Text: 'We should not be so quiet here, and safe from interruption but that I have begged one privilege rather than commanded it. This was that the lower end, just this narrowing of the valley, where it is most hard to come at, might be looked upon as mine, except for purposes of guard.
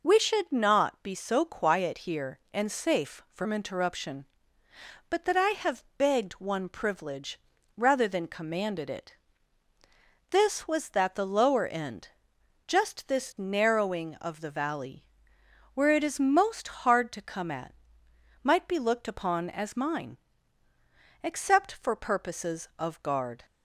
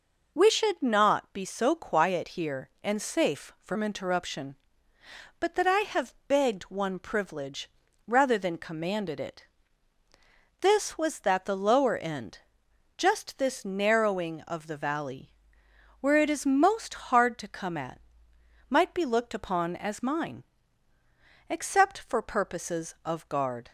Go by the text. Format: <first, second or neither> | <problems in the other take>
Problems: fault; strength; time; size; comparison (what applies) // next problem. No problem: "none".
neither | pauses between "privilege" and "rather"; the same in both